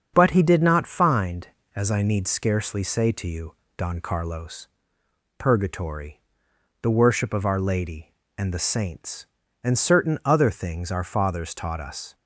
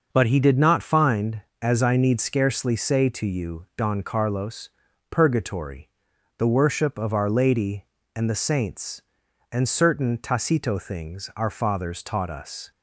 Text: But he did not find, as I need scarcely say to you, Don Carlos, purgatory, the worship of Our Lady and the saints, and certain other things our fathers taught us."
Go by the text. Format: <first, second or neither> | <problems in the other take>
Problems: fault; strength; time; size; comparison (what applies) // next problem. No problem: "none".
first | starts louder than the rest; noticeable; until 1.1 s; 6 dB; also in the first // says "tacito" for "other"; at 10.1 s